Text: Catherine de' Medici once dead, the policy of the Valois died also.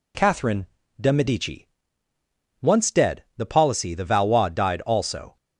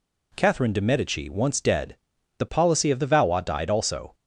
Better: second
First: pauses between "Catherine" and "de"; slight; at 0.6 s; 0.32 s long // pauses between "Medici" and "once"; noticeable; at 1.6 s; 0.94 s long // skips "of"; at 3.9 s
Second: none

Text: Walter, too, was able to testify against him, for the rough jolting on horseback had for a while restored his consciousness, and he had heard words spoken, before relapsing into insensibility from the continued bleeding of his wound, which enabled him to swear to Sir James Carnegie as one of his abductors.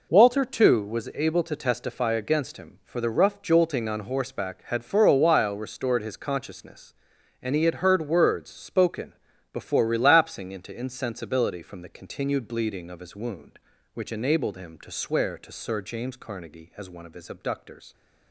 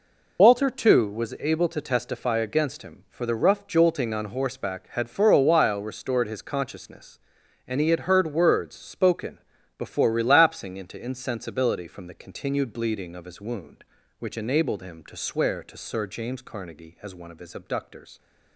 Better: first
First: none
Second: loses the start of "Walter"; at 0.3 s; 45 ms

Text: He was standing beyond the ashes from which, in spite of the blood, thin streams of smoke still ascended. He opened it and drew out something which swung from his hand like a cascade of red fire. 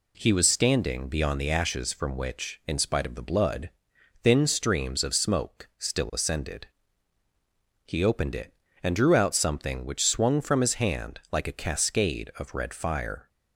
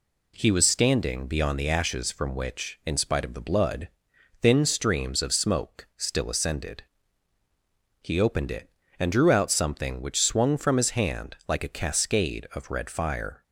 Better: neither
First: none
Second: none

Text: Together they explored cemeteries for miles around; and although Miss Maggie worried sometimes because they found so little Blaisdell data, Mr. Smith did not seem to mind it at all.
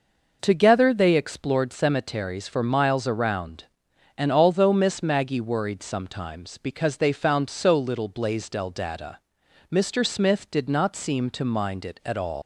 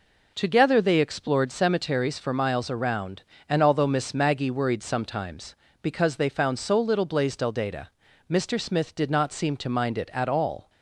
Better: second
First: leaves "all" unfinished; at 12.4 s; 140 ms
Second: none

